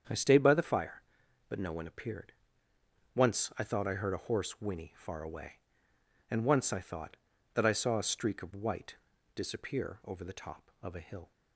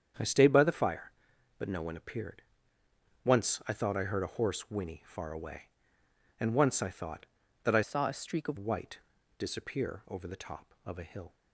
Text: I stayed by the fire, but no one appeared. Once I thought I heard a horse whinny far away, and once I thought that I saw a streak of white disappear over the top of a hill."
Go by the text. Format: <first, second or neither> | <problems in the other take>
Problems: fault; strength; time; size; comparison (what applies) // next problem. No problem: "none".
first | starts louder than the rest; strong; until 1.6 s; 8 dB; strong in the first // changes voice from "saw" to "of"; from 7.8 to 8.5 s; 0.7 s long // pauses between "white" and "disappear"; at 8.9 s; 0.40 s long; also in the first